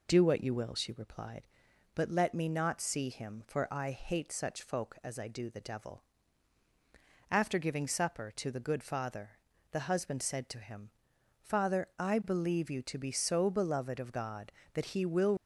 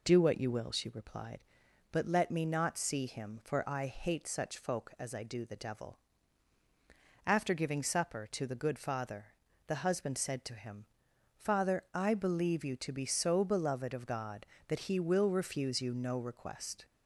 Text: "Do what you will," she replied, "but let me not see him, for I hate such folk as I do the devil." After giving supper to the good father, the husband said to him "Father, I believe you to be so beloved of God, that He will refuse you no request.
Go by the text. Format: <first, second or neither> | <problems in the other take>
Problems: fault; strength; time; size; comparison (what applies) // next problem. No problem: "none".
second | pauses between "him" and "Father"; noticeable; at 10.8 s; 0.50 s long; noticeable in the second // stops before "refuse you no request"; at 15.3 s